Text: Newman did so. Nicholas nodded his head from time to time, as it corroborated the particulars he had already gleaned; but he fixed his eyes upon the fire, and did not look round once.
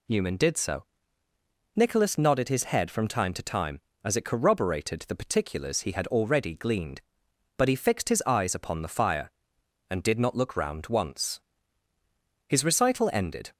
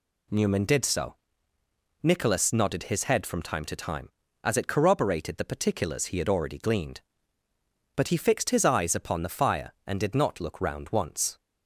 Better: second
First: goes on to say "His recital ended"; noticeable; from 12.4 s on; 1.0 s long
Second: none

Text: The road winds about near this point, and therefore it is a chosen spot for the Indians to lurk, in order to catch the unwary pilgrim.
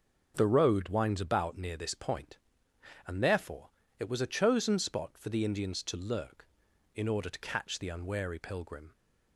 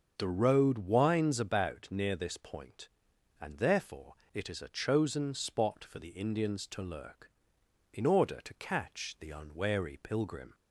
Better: second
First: starts louder than the rest; until 1.3 s; 6.5 dB // pauses between "therefore" and "it"; slight; at 3.6 s; 0.30 s long // says "was" for "is"; at 4.0 s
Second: starts louder than the rest; until 1.1 s; 6.5 dB // pauses between "therefore" and "it"; slight; at 4.1 s; 0.18 s long

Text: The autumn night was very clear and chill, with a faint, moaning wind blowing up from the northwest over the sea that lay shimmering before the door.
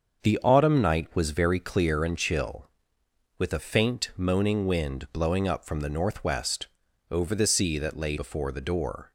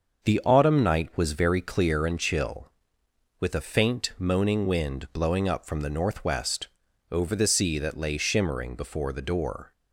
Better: second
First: starts louder than the rest; until 1.3 s; 7 dB // pauses between "northwest" and "over"; at 6.6 s; 0.44 s long // skips "shimmering"; at 8.1 s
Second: starts louder than the rest; until 1.3 s; 6.5 dB // pauses between "northwest" and "over"; at 6.6 s; 0.44 s long

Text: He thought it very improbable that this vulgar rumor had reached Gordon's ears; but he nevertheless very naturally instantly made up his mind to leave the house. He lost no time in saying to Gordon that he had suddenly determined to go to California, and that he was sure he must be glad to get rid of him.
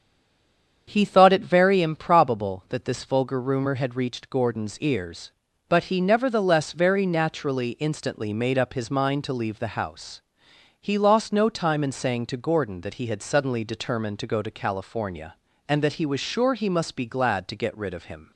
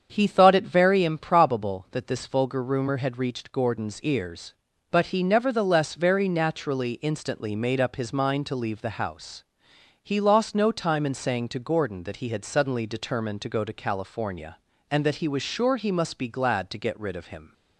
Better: second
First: stays silent before the first word; slight; until 0.8 s; 0.8 s long // starts louder than the rest; strong; until 1.8 s; 7.5 dB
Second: starts louder than the rest; strong; until 1.1 s; 7.5 dB

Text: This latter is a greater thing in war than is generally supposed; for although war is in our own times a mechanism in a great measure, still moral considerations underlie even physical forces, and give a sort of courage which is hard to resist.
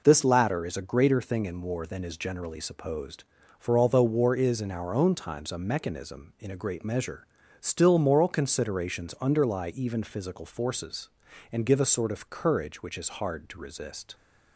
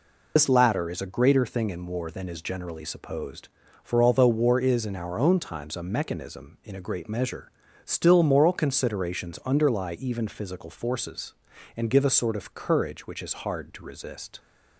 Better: first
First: none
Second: loses the start of "This"; at 0.3 s; 65 ms

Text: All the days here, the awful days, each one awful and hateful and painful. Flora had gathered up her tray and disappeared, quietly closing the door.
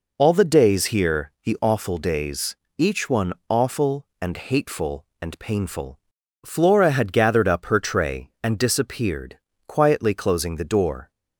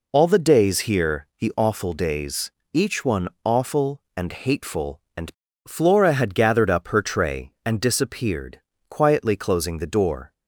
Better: first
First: pauses between "one" and "awful"; slight; at 3.3 s; 0.16 s long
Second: pauses between "one" and "awful"; slight; at 3.2 s; 0.16 s long // skips "painful"; at 5.4 s

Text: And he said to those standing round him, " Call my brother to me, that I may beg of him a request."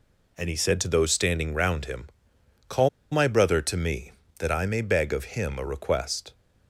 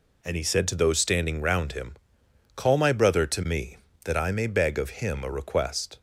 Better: second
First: pauses between "Call" and "my"; slight; at 2.8 s; 0.23 s long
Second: none

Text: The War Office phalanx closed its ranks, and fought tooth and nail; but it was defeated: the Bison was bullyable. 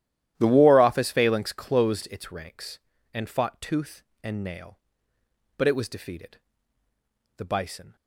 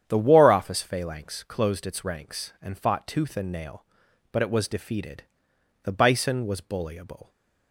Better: second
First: starts louder than the rest; strong; until 1.3 s; 12.5 dB // stops before "was bullyable"; at 7.9 s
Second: starts louder than the rest; strong; until 1.0 s; 9 dB

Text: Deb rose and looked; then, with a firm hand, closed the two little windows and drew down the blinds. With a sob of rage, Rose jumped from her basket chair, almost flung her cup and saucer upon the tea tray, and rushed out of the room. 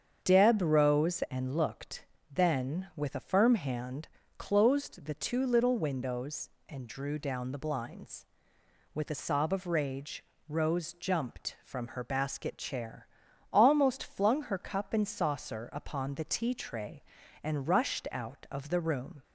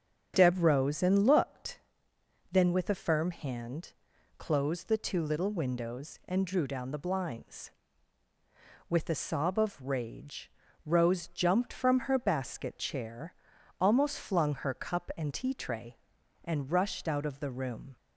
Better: first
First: starts louder than the rest; strong; until 1.2 s; 7.5 dB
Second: starts louder than the rest; strong; until 1.3 s; 7.5 dB // skips "saucer upon the"; at 15.3 s

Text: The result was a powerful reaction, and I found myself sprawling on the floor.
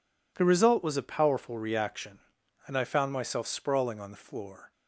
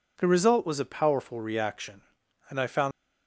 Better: first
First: none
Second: stops before "myself sprawling on the floor"; at 2.9 s

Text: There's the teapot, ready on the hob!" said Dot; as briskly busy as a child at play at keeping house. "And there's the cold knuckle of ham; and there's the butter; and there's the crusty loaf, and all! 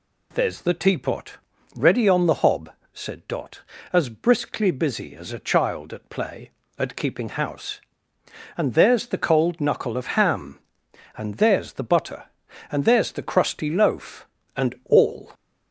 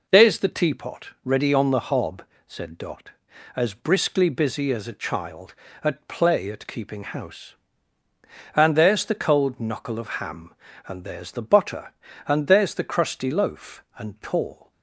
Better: first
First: none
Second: says "tall" for "all"; at 14.2 s

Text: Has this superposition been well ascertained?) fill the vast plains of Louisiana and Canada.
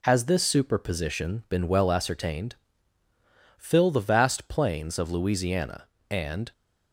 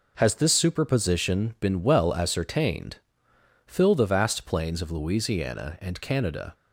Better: second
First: stops before "Canada"; at 6.5 s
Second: none

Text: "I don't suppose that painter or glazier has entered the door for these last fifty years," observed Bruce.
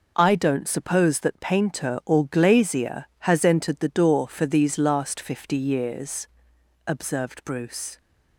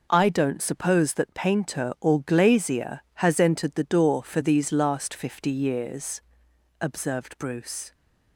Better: neither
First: none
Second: none

